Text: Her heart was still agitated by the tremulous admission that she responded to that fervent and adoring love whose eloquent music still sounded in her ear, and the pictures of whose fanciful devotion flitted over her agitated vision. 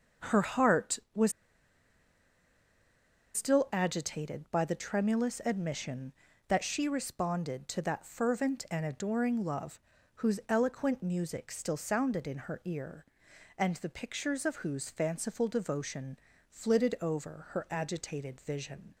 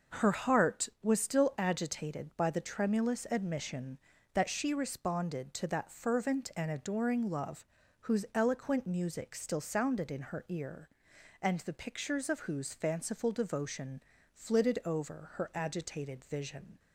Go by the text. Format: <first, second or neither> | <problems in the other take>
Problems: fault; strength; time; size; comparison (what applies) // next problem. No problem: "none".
second | starts louder than the rest; noticeable; until 3.4 s; 6 dB; also in the second // pauses between "was" and "still"; strong; at 1.3 s; 2.0 s long // pauses between "love" and "whose"; slight; at 9.7 s; 0.36 s long; slight in the second // pauses between "devotion" and "flitted"; slight; at 16.1 s; 0.32 s long; slight in the second